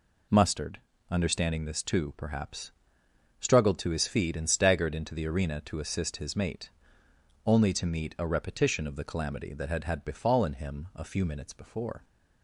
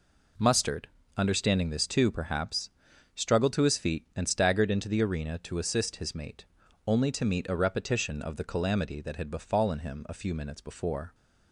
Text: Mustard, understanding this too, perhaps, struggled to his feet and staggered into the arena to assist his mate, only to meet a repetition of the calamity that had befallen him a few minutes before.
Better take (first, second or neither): second